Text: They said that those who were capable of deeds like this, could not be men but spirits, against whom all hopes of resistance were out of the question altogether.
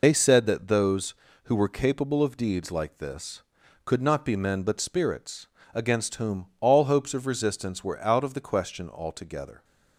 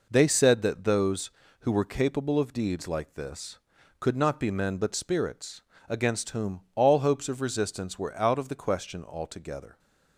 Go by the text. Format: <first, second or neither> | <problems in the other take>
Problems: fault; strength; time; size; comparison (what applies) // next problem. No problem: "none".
second | loses the start of "They"; at 0.0 s; 75 ms